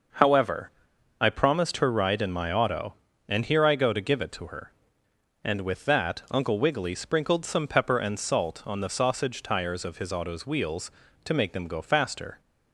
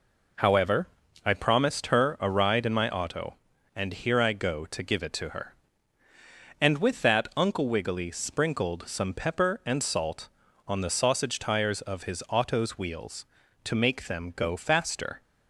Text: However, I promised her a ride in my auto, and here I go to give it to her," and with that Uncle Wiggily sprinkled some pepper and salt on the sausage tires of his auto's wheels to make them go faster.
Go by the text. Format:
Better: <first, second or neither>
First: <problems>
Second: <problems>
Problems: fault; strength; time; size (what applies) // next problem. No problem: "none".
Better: second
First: skips "a"; at 1.9 s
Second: none